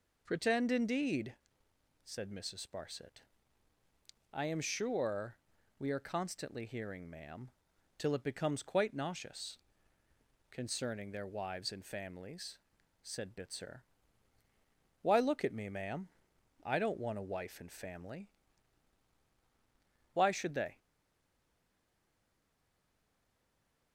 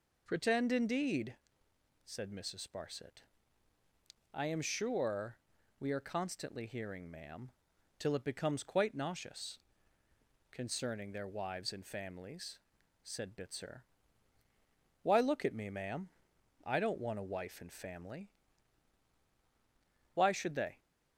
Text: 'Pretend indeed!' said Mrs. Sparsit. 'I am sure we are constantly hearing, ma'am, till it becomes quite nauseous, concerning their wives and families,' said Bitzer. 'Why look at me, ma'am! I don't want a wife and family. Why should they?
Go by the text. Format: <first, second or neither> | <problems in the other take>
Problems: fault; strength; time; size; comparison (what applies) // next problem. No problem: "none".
second | pauses between "sure" and "we"; at 5.3 s; 0.42 s long; also in the second // stays silent after the last word; strong; from 20.7 s on; 3.2 s long